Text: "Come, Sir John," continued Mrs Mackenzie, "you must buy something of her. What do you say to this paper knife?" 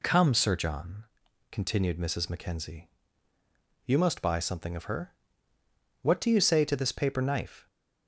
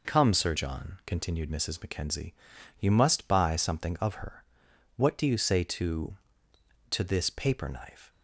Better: first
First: none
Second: says "to" twice; at 6.9 s

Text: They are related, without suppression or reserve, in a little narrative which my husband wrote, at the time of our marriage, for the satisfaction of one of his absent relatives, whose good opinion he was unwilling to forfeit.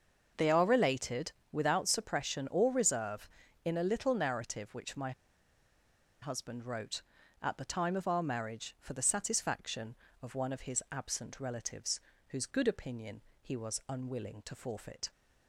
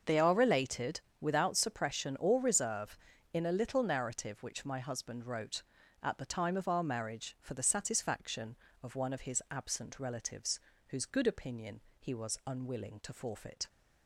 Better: second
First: starts louder than the rest; until 1.5 s; 6.5 dB // pauses between "my" and "husband"; at 5.1 s; 1.1 s long // pauses between "opinion" and "he"; slight; at 13.2 s; 0.20 s long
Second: starts louder than the rest; until 1.2 s; 6.5 dB // pauses between "opinion" and "he"; slight; at 11.8 s; 0.18 s long

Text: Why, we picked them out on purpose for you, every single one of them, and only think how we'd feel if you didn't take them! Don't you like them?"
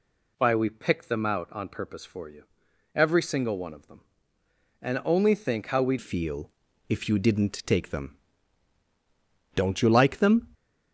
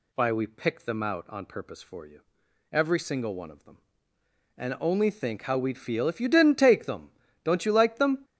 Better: second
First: changes voice at "feel"; from 6.0 s on; 4.4 s long // pauses between "feel" and "if"; at 6.5 s; 0.38 s long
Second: none

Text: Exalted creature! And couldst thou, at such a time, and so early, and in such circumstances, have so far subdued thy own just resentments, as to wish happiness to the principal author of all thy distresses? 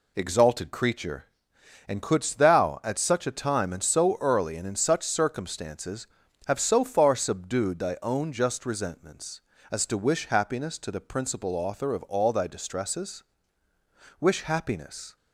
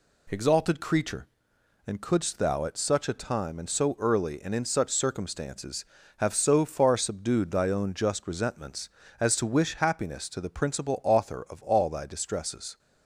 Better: second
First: goes on to say "Wish happiness"; noticeable; from 14.1 s on; 0.96 s long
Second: none

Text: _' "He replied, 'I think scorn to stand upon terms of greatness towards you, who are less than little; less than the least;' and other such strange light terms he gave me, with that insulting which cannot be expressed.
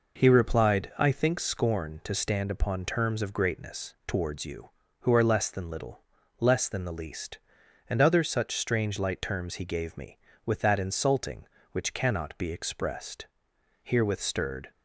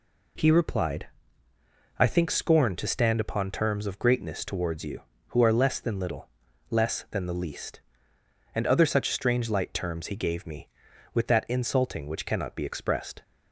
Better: second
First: goes on to say "Herewith stirred"; noticeable; from 13.8 s on; 0.88 s long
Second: none

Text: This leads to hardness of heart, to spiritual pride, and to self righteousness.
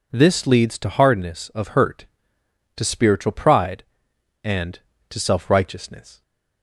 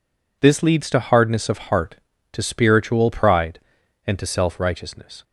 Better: second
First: says "hurt" for "heart"; at 1.6 s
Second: none

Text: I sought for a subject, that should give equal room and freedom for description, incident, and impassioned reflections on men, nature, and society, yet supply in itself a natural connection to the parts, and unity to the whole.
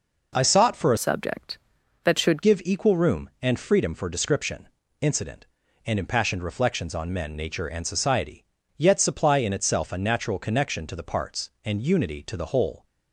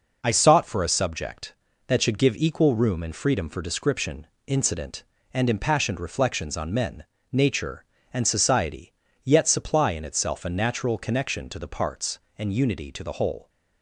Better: second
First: changes voice from "subject" to "should"; from 0.9 to 2.4 s; 1.5 s long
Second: none

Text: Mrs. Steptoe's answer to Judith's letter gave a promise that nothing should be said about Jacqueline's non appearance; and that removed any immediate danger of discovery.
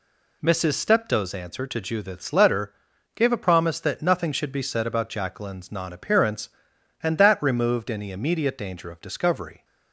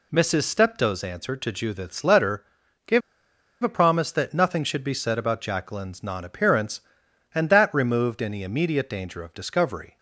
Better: first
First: pauses between "letter" and "gave"; at 2.7 s; 0.42 s long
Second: pauses between "letter" and "gave"; at 2.4 s; 0.42 s long // pauses between "gave" and "a"; noticeable; at 3.0 s; 0.62 s long

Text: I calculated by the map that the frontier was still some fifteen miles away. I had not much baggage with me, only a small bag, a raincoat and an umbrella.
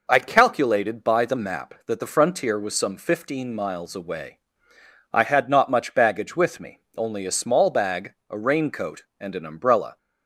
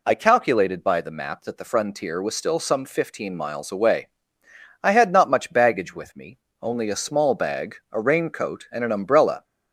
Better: second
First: skips "still"; at 2.7 s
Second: none

